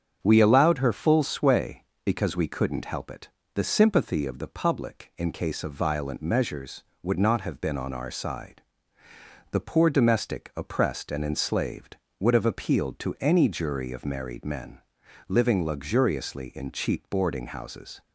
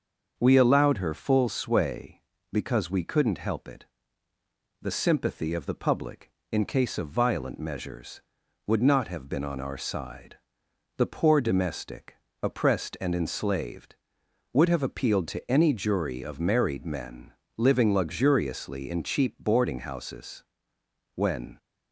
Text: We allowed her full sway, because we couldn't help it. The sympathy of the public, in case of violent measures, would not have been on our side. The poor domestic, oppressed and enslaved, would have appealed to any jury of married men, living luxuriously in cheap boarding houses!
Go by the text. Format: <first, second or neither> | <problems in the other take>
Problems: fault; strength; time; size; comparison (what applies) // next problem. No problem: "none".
first | starts louder than the rest; until 1.3 s; 6.5 dB; strong in the first // goes on to say "When"; slight; from 21.1 s on; 0.44 s long